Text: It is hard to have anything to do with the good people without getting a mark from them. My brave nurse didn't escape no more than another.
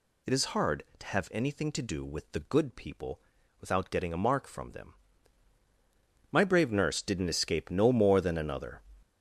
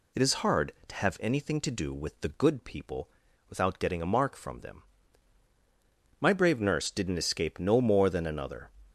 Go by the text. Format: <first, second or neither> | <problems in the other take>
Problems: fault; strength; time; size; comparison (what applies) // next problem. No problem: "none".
second | gets louder; strong; throughout; 8 dB // pauses between "people" and "without"; at 3.1 s; 0.40 s long; also in the second